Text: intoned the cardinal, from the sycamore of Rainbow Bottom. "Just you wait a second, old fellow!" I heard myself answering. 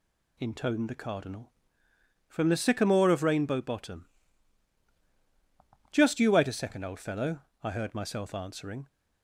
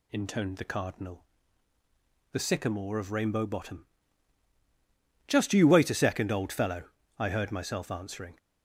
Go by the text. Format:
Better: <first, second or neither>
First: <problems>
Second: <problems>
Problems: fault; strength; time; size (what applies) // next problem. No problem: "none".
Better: first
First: none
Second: skips "from"; at 1.7 s